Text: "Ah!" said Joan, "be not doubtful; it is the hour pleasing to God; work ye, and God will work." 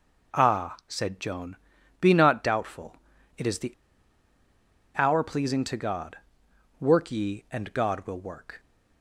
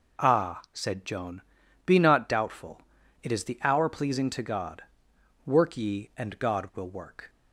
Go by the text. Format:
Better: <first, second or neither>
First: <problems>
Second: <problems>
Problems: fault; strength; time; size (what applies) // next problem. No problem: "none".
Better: second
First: pauses between "the" and "hour"; strong; at 3.7 s; 1.2 s long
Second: none